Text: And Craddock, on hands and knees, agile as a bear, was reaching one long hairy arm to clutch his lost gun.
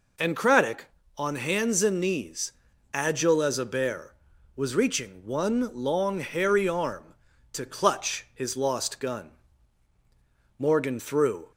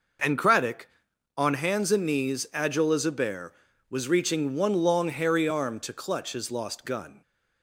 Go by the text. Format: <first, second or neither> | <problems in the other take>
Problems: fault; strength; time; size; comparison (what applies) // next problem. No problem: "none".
second | goes on to say "Morgan threw"; noticeable; from 10.5 s on; 0.92 s long